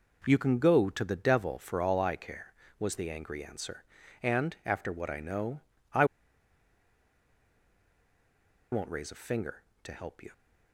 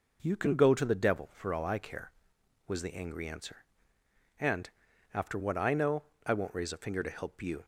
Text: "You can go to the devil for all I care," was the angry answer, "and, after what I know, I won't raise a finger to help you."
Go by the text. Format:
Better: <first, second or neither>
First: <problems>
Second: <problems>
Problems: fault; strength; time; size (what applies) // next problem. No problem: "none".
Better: second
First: pauses between "I" and "won't"; strong; at 6.0 s; 2.6 s long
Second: none